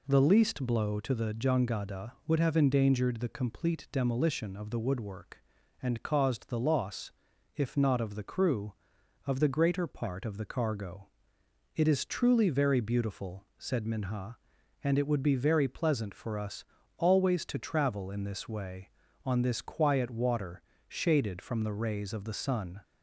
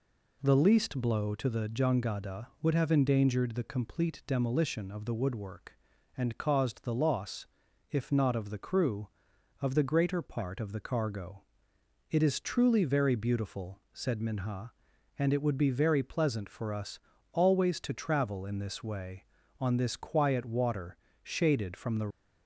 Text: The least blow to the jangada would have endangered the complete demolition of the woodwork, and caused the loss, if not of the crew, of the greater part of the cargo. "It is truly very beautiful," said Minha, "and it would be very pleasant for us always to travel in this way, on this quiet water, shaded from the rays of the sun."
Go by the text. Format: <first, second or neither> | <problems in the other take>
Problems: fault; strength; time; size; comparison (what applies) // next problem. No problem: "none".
first | pauses between "us" and "always"; slight; at 16.9 s; 0.32 s long; slight in the first // stops before "rays of the sun"; at 22.0 s